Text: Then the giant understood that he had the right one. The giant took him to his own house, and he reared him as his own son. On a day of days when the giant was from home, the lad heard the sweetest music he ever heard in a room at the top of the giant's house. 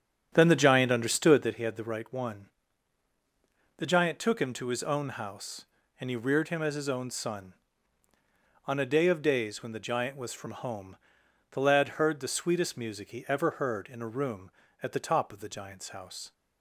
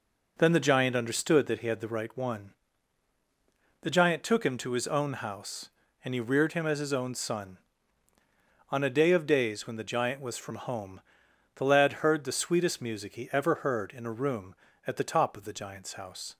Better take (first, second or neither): second